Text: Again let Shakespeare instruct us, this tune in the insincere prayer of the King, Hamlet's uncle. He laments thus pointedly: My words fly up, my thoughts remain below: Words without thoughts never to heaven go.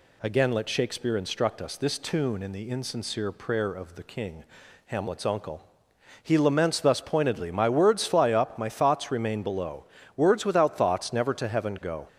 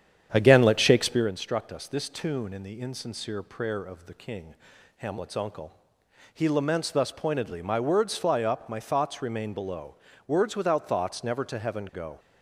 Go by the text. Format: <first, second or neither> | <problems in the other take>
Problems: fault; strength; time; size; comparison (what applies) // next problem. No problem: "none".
first | starts louder than the rest; strong; until 1.3 s; 9 dB